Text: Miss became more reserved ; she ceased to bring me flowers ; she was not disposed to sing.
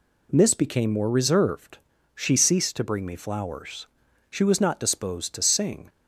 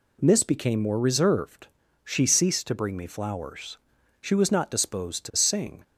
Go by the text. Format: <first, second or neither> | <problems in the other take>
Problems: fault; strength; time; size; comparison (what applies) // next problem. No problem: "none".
neither | none